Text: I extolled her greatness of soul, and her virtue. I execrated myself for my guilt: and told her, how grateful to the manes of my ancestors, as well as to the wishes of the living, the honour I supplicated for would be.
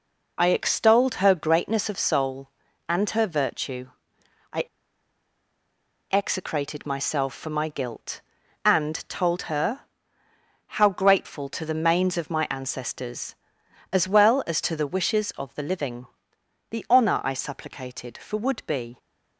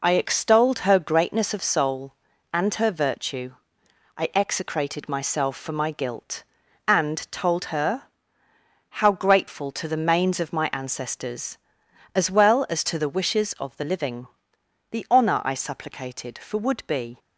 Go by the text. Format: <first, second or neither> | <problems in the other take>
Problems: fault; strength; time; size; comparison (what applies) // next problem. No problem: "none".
second | pauses between "I" and "execrated"; strong; at 4.6 s; 1.4 s long